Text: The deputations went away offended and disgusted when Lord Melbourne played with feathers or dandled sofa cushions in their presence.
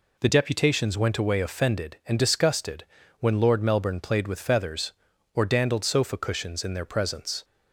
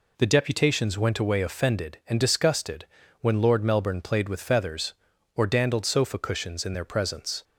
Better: neither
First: pauses between "disgusted" and "when"; slight; at 2.8 s; 0.34 s long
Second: pauses between "disgusted" and "when"; slight; at 2.8 s; 0.34 s long

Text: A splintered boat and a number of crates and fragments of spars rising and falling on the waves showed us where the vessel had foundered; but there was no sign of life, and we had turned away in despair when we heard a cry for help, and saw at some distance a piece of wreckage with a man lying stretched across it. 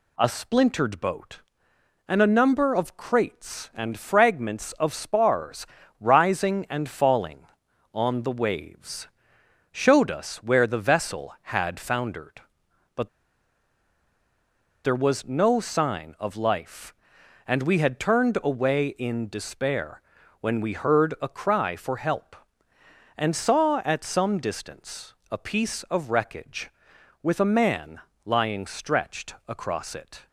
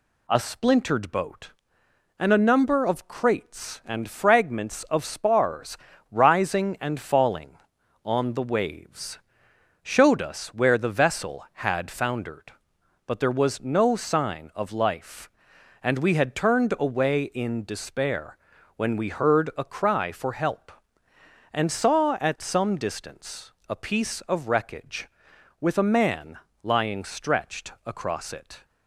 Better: second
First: pauses between "spars" and "rising"; slight; at 5.6 s; 0.34 s long // pauses between "waves" and "showed"; noticeable; at 9.0 s; 0.64 s long // pauses between "but" and "there"; strong; at 13.0 s; 1.7 s long // pauses between "despair" and "when"; at 19.9 s; 0.42 s long // pauses between "distance" and "a"; slight; at 25.1 s; 0.16 s long // pauses between "man" and "lying"; slight; at 27.9 s; 0.26 s long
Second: pauses between "spars" and "rising"; slight; at 5.7 s; 0.34 s long // pauses between "waves" and "showed"; noticeable; at 9.1 s; 0.64 s long // pauses between "despair" and "when"; at 18.3 s; 0.42 s long // pauses between "distance" and "a"; slight; at 23.5 s; 0.16 s long // pauses between "man" and "lying"; slight; at 26.3 s; 0.26 s long

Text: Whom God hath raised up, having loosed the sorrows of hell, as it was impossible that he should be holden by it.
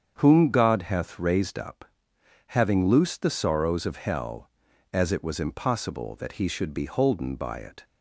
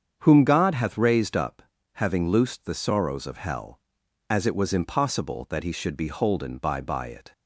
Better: first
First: starts louder than the rest; strong; until 1.2 s; 7.5 dB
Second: starts louder than the rest; strong; until 1.2 s; 7.5 dB // says "by" twice; at 6.8 s

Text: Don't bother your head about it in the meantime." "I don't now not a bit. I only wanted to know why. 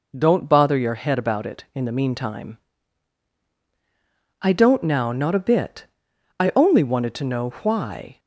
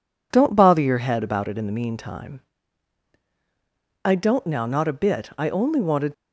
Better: first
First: none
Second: stops before "to know why"; at 6.1 s

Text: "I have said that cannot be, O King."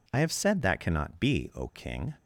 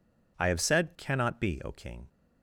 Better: first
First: none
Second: skips "that"; at 0.9 s

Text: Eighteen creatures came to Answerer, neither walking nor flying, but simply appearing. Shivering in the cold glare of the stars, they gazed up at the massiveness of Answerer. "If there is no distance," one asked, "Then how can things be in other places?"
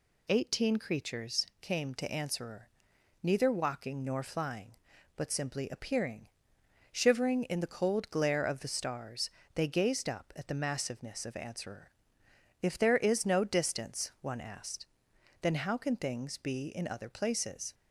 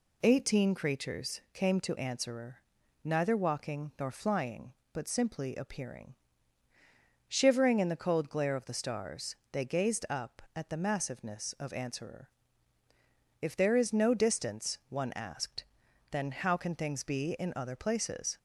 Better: neither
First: none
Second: none

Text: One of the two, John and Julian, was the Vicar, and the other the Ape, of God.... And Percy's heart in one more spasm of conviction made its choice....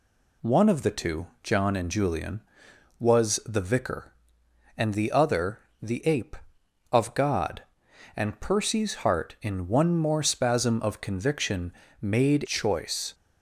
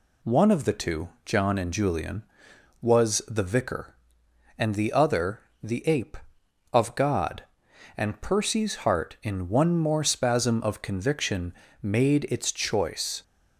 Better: second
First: pauses between "other" and "the"; slight; at 5.5 s; 0.22 s long // pauses between "conviction" and "made"; slight; at 11.7 s; 0.30 s long // skips "its"; at 12.4 s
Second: pauses between "other" and "the"; slight; at 5.4 s; 0.22 s long // pauses between "conviction" and "made"; slight; at 11.5 s; 0.30 s long

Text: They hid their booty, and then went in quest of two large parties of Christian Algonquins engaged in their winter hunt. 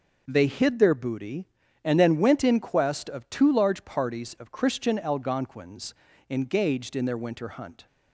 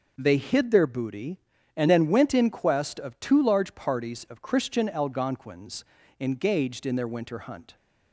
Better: neither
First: pauses between "Algonquins" and "engaged"; slight; at 5.9 s; 0.36 s long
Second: pauses between "Algonquins" and "engaged"; slight; at 5.8 s; 0.36 s long

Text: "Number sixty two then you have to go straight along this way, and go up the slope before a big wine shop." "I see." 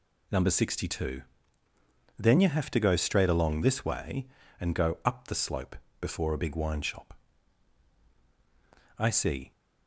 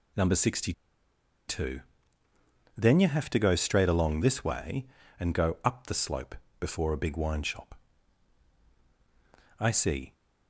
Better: first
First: pauses between "two" and "then"; noticeable; at 1.2 s; 0.98 s long // pauses between "slope" and "before"; slight; at 5.7 s; 0.26 s long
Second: pauses between "sixty" and "two"; noticeable; at 0.7 s; 0.76 s long // pauses between "two" and "then"; noticeable; at 1.8 s; 0.98 s long // pauses between "slope" and "before"; slight; at 6.3 s; 0.26 s long

